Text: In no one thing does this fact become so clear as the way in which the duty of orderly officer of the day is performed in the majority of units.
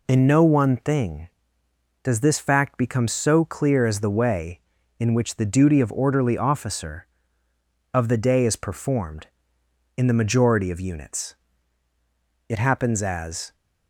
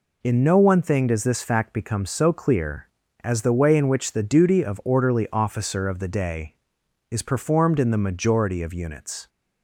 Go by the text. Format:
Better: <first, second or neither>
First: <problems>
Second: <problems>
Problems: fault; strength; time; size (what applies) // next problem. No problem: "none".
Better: second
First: goes on to say "It happens as"; noticeable; from 12.4 s on; 1.0 s long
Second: none